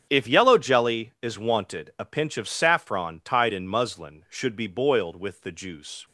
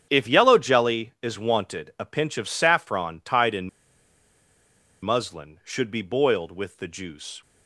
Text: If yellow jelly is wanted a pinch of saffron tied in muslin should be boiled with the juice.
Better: first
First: starts louder than the rest; strong; until 1.1 s; 8 dB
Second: starts louder than the rest; strong; until 1.1 s; 8 dB // pauses between "in" and "muslin"; strong; at 3.6 s; 1.3 s long

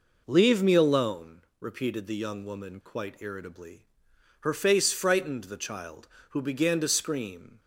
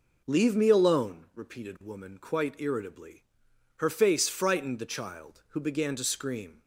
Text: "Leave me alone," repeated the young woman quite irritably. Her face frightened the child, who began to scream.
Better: first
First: none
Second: skips "the young"; at 1.7 s

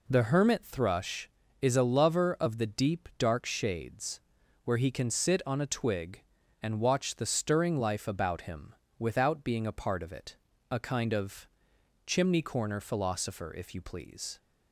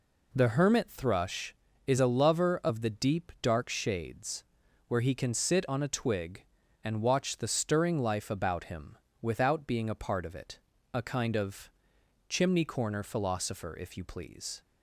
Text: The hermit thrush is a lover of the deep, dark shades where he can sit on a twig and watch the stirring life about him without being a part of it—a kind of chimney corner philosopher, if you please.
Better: neither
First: pauses between "shades" and "where"; at 4.2 s; 0.42 s long // pauses between "him" and "without"; slight; at 8.7 s; 0.24 s long // pauses between "of" and "chimney"; noticeable; at 11.4 s; 0.58 s long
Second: pauses between "shades" and "where"; at 4.4 s; 0.42 s long // pauses between "him" and "without"; slight; at 8.9 s; 0.24 s long // pauses between "of" and "chimney"; noticeable; at 11.7 s; 0.58 s long

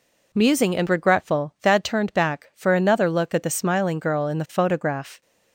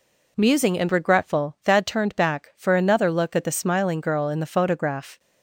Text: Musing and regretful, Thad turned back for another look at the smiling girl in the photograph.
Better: neither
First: none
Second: none

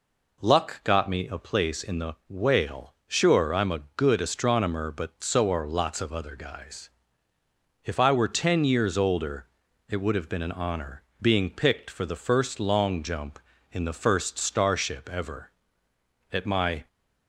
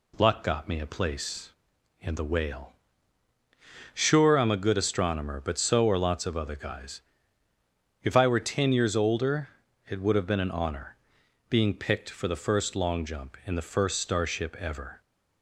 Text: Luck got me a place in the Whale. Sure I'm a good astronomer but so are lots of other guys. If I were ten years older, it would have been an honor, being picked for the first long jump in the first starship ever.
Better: second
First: goes on to say "At my"; from 16.3 s on; 0.56 s long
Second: none

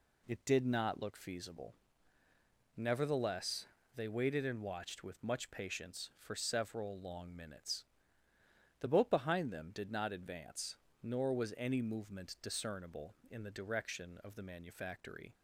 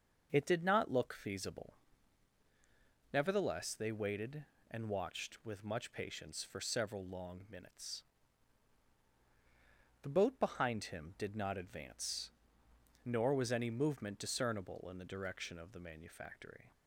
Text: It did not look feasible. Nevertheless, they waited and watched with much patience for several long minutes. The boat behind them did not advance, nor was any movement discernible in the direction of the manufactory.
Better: first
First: none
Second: starts louder than the rest; until 1.3 s; 6 dB // says "him" for "them"; at 10.8 s

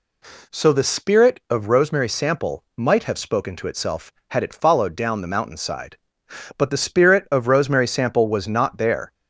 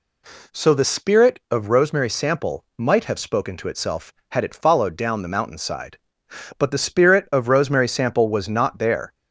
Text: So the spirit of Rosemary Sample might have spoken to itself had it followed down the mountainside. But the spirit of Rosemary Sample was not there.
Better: neither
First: none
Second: none

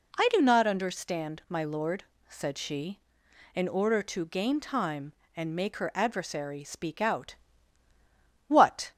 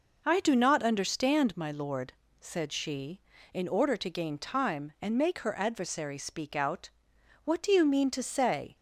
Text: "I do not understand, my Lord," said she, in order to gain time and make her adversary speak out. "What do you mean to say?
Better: second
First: stops before "do you mean to say"; at 8.9 s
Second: none

